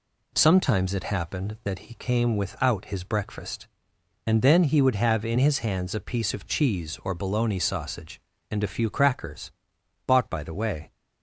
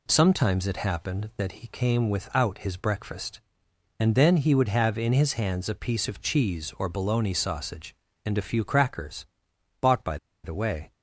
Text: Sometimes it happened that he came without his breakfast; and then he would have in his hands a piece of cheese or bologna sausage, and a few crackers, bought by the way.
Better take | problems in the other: first | pauses between "by" and "the"; slight; at 10.1 s; 0.27 s long

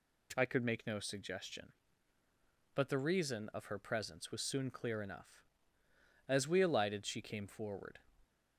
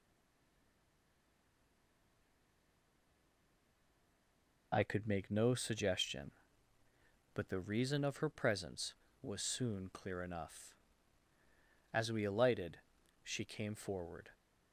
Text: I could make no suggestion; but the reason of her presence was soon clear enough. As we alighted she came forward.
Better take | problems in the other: first | stays silent before the first word; strong; until 4.7 s; 4.7 s long // pauses between "alighted" and "she"; noticeable; at 12.7 s; 0.48 s long

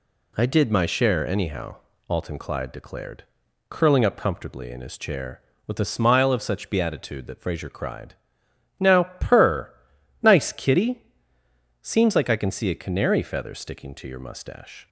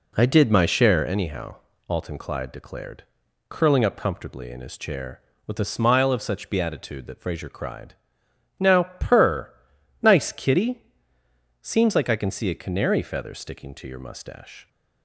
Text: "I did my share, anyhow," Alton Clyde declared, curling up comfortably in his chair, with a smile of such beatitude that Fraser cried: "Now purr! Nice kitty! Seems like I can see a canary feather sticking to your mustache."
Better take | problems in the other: first | starts louder than the rest; slight; until 1.1 s; 2.5 dB // pauses between "Now" and "purr"; slight; at 8.8 s; 0.16 s long; slight in the first

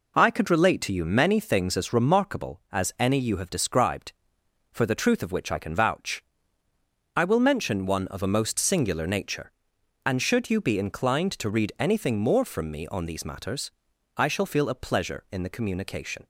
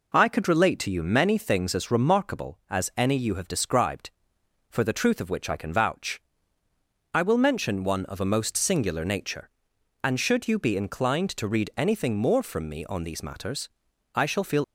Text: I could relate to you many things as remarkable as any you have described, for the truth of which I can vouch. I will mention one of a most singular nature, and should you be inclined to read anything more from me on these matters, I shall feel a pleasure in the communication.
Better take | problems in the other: first | stops before "a pleasure in the communication"; at 14.6 s

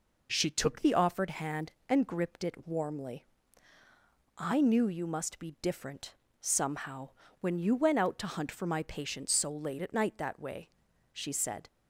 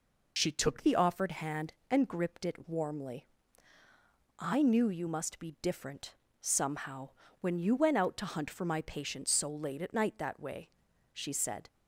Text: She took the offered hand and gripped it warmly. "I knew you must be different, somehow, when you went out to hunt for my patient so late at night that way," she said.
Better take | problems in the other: first | loses the start of "She"; at 0.3 s; 50 ms

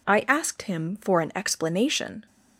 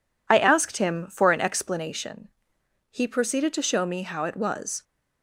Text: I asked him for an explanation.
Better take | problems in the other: first | goes on to say "He proceeded to show me how it was"; strong; from 2.8 s on; 1.9 s long

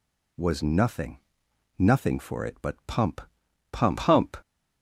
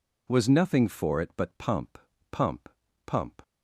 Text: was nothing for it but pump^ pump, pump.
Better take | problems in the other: second | says "nothing" twice; at 1.7 s // pauses between "pump" and "pump"; noticeable; at 3.2 s; 0.50 s long; slight in the second

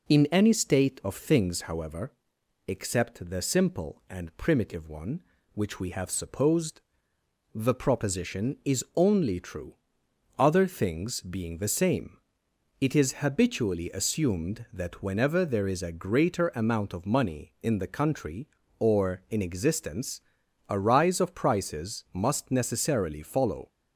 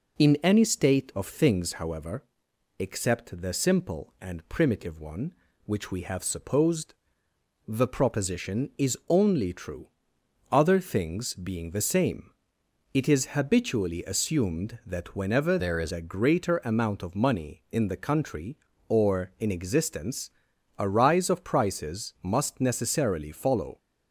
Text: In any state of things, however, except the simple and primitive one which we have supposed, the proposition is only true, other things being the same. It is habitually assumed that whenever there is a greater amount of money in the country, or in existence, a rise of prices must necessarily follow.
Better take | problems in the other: first | changes voice from "there" to "is"; from 15.5 to 15.9 s; 0.4 s long

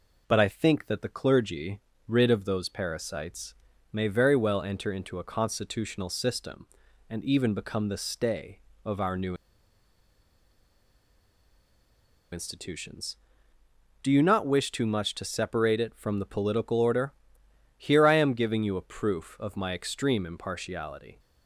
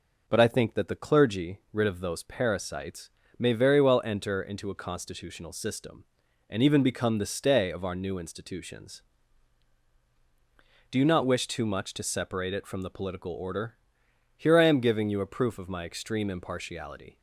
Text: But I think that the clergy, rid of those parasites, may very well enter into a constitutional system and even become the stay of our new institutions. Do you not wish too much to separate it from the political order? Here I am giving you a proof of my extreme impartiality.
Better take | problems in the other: second | pauses between "new" and "institutions"; strong; at 9.3 s; 2.9 s long

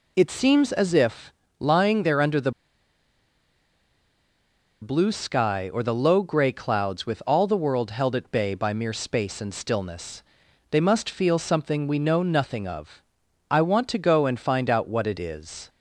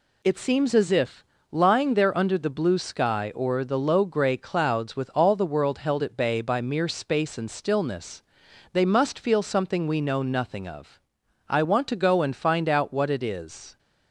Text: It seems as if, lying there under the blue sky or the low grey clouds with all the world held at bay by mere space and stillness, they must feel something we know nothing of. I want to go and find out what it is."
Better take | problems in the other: second | pauses between "the" and "blue"; strong; at 2.5 s; 2.3 s long

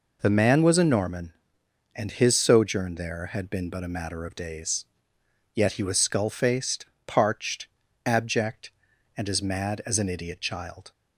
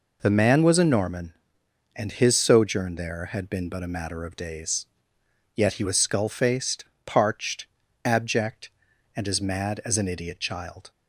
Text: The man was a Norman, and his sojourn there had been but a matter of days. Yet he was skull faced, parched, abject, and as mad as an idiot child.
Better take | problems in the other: neither | none

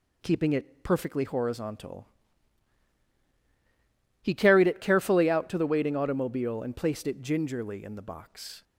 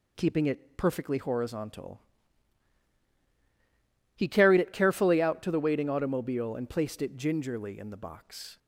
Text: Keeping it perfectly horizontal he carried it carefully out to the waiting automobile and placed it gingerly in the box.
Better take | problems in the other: neither | pauses between "horizontal" and "he"; strong; the same in both

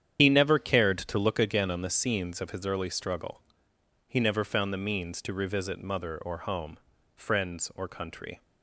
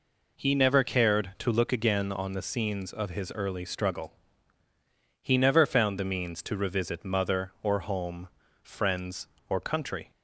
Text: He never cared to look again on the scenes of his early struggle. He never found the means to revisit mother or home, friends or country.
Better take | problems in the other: second | loses the start of "He"; at 0.1 s; 85 ms // starts louder than the rest; strong; until 1.2 s; 9 dB

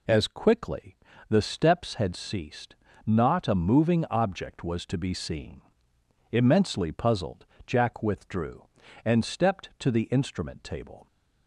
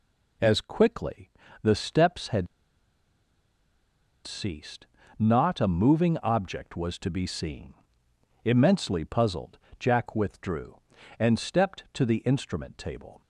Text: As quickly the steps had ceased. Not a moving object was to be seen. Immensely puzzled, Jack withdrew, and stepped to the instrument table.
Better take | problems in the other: first | pauses between "quickly" and "the"; slight; at 1.3 s; 0.32 s long; slight in the first // pauses between "had" and "ceased"; strong; at 2.4 s; 1.7 s long

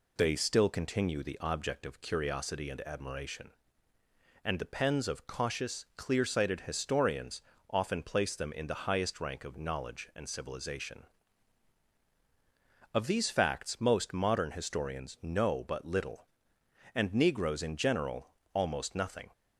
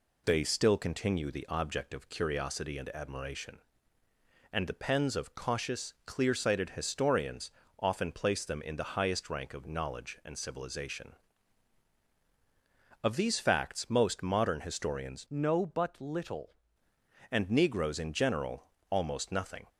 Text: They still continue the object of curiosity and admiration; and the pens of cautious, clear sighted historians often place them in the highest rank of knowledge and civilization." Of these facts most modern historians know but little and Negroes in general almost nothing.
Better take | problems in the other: first | pauses between "historians" and "often"; slight; at 7.4 s; 0.28 s long; slight in the first // changes voice from "know" to "little"; from 15.2 to 16.5 s; 1.3 s long // pauses between "general" and "almost"; slight; at 18.6 s; 0.26 s long; slight in the first

